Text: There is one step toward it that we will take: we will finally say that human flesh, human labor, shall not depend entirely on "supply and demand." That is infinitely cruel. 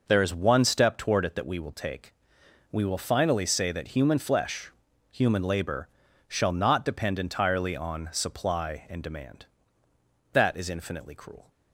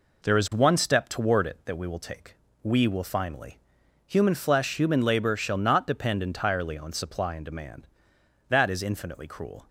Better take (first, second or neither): first